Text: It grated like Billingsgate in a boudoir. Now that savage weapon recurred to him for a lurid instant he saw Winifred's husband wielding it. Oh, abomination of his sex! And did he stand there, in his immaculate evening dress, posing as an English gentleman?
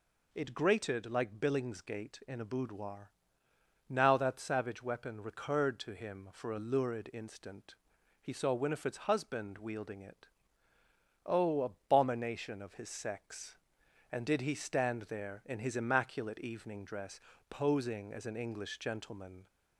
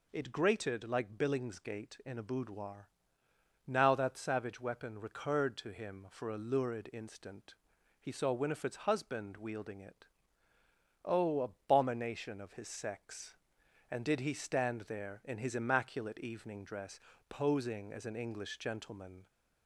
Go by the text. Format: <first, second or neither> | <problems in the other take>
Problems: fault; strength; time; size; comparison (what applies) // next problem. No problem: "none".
neither | pauses between "instant" and "he"; noticeable; the same in both